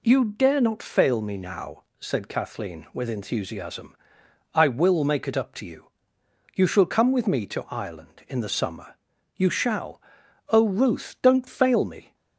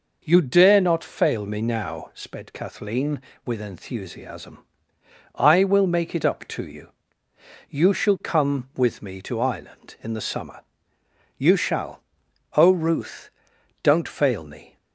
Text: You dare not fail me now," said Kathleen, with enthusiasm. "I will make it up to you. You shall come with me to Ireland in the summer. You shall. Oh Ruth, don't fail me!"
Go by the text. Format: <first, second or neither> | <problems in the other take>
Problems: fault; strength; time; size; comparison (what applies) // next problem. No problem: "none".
first | says "sped" for "said"; at 2.1 s